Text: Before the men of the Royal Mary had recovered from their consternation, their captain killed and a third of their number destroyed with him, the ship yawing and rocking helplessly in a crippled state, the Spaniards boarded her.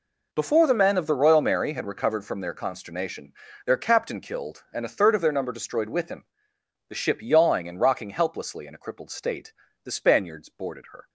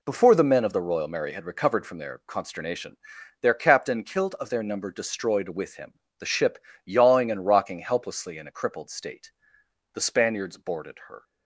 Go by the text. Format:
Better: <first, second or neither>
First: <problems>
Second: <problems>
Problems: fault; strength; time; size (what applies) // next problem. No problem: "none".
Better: first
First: none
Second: skips "and a third"; at 4.3 s // pauses between "ship" and "yawing"; slight; at 6.5 s; 0.28 s long